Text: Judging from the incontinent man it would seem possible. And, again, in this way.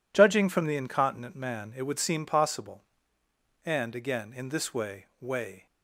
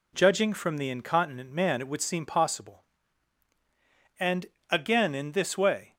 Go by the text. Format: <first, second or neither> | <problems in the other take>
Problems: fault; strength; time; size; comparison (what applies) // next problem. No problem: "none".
second | says "way" twice; at 5.1 s